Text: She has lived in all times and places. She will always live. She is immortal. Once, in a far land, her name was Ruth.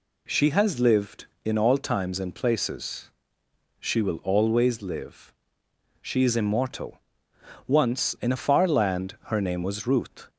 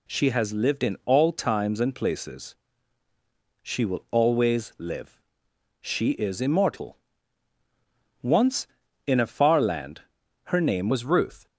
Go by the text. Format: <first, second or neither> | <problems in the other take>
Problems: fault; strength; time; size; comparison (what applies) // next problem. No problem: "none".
first | changes voice at "was"; from 10.9 s on; 0.5 s long